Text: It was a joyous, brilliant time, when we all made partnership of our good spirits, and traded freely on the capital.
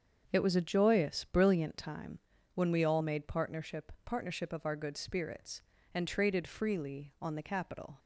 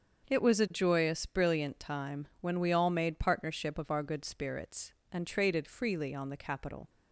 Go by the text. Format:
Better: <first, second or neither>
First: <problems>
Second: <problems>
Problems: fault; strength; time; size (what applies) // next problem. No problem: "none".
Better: second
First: starts louder than the rest; until 1.3 s; 7 dB // says "partnership" twice; at 4.0 s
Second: starts louder than the rest; until 1.3 s; 6.5 dB